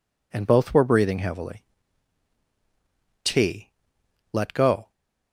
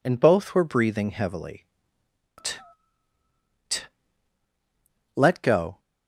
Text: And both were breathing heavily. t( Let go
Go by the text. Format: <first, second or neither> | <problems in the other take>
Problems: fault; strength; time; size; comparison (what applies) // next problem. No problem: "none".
first | says "t" twice; at 3.6 s